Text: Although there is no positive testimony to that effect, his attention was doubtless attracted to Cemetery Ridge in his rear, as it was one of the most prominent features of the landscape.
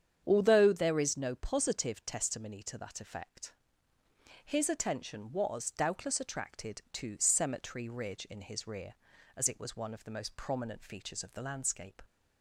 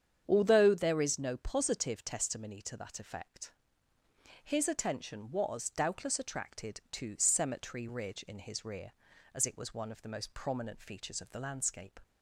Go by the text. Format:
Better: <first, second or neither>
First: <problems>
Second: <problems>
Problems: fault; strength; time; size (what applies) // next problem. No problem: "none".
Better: neither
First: starts louder than the rest; strong; until 1.2 s; 8 dB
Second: starts louder than the rest; strong; until 1.2 s; 8 dB